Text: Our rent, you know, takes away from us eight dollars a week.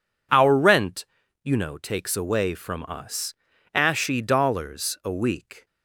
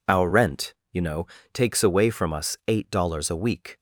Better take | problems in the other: second | says "ashy" for "eight"; at 3.7 s

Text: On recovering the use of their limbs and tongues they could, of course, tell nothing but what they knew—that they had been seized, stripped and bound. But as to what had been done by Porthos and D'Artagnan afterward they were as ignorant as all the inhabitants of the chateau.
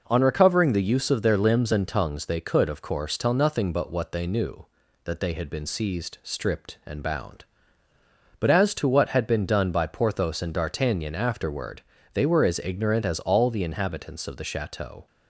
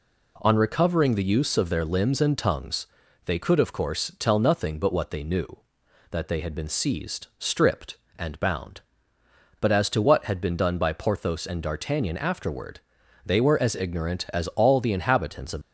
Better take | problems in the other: first | pauses between "tongues" and "they"; at 2.8 s; 0.38 s long // pauses between "afterward" and "they"; noticeable; at 12.7 s; 0.48 s long; slight in the first // stops before "the chateau"; at 15.6 s

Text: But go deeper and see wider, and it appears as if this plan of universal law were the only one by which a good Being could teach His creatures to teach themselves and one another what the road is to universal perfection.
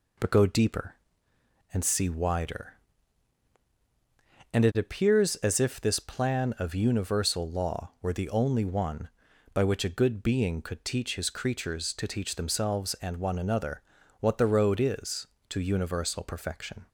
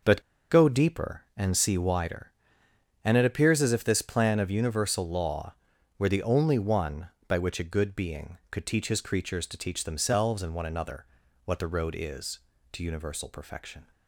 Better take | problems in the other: first | starts louder than the rest; noticeable; until 1.4 s; 6 dB // pauses between "But" and "go"; slight; at 0.2 s; 0.30 s long // pauses between "another" and "what"; at 11.0 s; 0.42 s long; slight in the first

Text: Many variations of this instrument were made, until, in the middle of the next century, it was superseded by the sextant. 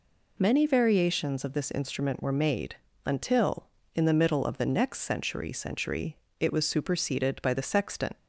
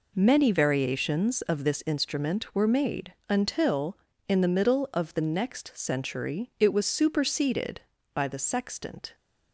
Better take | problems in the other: second | says "century" twice; at 5.5 s

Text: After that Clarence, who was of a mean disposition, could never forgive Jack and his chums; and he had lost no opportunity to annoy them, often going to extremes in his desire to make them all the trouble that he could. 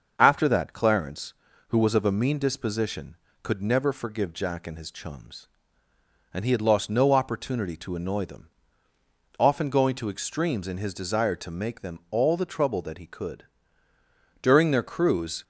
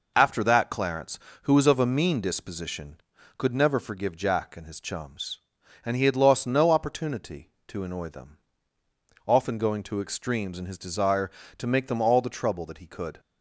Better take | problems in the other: second | starts louder than the rest; until 1.1 s; 6.5 dB // goes on to say "During their cruise"; noticeable; from 14.4 s on; 1.0 s long

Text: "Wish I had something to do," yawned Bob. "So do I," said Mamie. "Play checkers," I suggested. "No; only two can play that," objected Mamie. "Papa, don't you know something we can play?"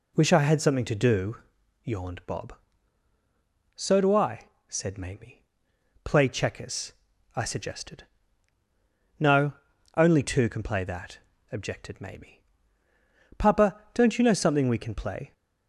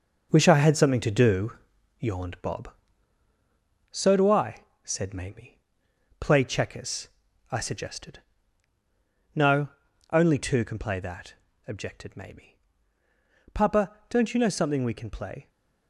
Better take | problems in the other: first | gets quieter; strong; throughout; 7.5 dB

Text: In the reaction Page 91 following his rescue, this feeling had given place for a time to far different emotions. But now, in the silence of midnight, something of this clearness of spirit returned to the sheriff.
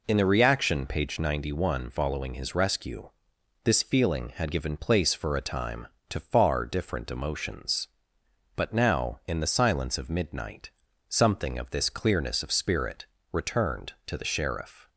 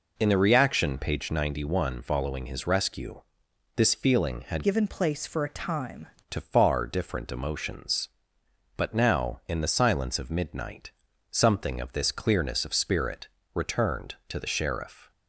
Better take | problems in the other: first | changes voice from "given" to "time"; from 4.6 to 6.0 s; 1.4 s long // pauses between "spirit" and "returned"; slight; at 13.2 s; 0.26 s long; slight in the first

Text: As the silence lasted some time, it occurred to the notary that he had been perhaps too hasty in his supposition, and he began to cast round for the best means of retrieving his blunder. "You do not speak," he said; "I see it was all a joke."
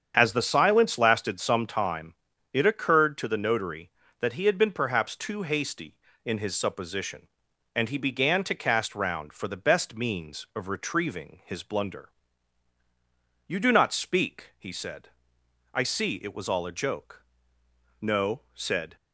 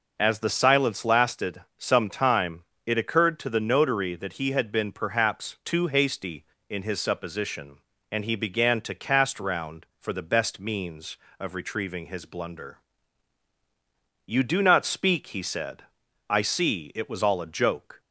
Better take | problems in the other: second | starts louder than the rest; strong; until 1.1 s; 8 dB // goes on to say "No said"; noticeable; from 17.9 s on; 0.96 s long

